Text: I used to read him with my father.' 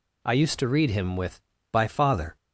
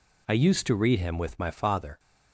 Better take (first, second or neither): second